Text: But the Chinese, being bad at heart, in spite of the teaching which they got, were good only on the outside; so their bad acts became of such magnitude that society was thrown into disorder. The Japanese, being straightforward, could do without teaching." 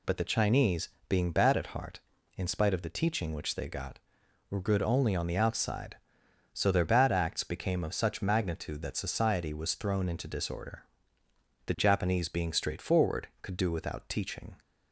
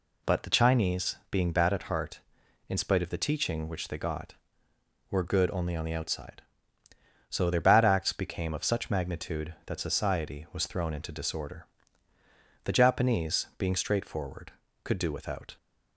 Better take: first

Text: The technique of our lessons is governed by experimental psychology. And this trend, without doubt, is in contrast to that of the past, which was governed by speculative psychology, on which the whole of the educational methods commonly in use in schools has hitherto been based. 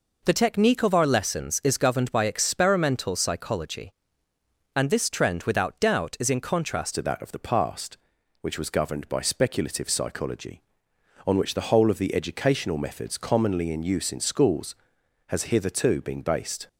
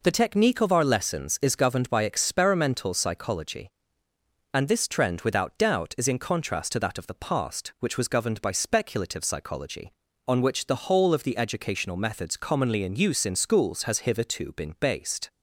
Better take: second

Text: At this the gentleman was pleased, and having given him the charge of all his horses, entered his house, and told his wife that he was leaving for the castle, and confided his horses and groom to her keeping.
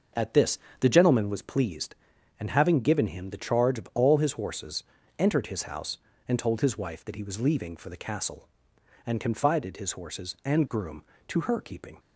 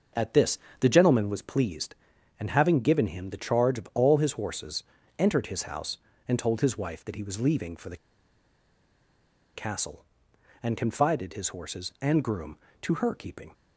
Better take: first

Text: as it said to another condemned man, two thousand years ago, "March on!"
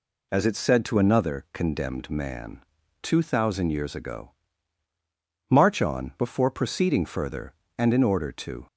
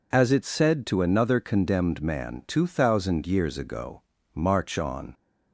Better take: second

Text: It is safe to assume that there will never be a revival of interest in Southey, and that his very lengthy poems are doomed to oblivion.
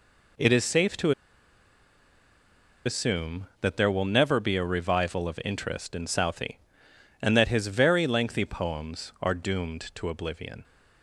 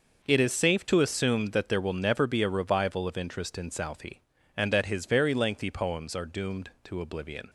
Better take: second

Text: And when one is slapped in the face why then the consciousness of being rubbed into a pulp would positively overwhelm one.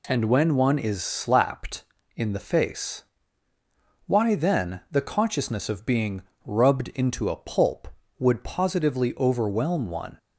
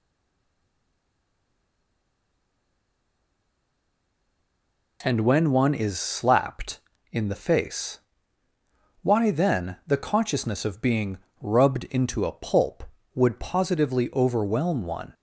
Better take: first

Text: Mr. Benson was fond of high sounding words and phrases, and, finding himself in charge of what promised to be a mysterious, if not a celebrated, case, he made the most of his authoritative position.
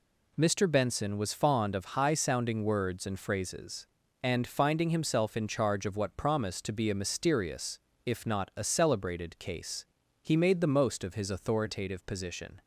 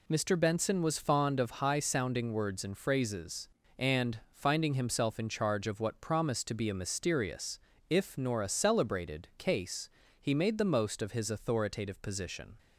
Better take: first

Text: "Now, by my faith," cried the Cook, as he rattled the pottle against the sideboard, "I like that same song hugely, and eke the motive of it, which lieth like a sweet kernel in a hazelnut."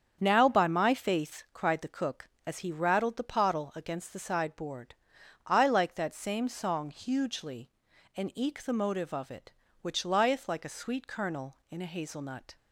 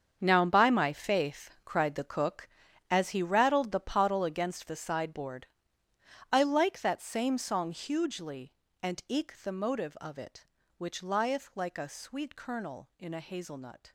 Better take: first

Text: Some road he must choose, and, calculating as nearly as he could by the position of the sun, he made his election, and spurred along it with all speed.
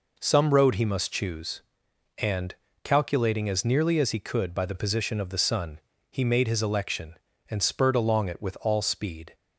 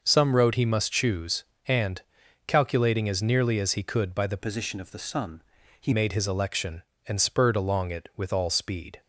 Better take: first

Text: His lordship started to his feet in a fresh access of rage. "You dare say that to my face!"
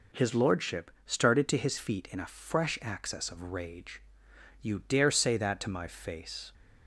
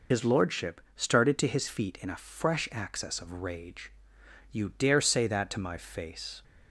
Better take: first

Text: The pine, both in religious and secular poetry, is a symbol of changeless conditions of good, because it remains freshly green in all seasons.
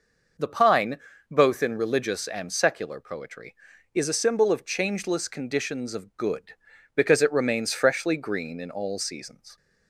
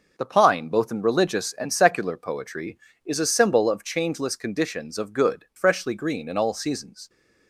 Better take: first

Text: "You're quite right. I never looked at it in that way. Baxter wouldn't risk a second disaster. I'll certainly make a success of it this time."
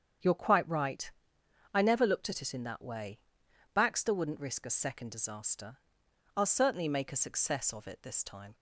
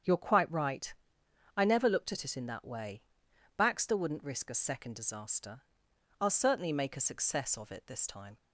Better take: neither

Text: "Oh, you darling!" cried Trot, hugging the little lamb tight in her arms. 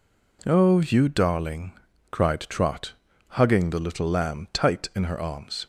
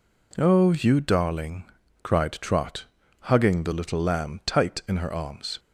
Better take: neither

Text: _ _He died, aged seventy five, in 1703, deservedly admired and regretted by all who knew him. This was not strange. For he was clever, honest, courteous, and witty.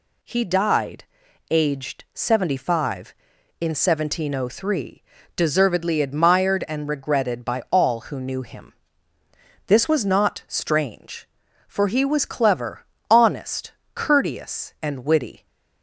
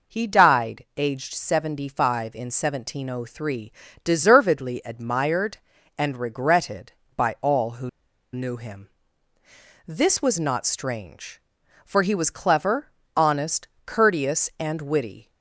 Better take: first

